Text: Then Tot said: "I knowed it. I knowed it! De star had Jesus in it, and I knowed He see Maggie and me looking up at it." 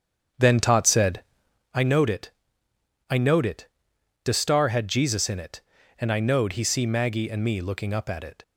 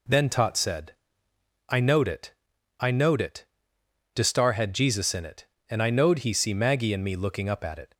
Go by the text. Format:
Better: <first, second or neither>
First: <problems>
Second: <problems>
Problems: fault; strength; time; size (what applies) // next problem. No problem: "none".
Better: second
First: starts louder than the rest; strong; until 1.7 s; 8 dB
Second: none